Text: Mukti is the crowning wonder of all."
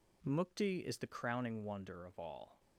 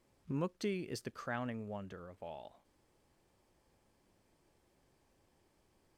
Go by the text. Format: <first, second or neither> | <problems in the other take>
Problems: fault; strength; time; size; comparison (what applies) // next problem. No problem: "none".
first | stays silent after the last word; strong; from 2.6 s on; 3.3 s long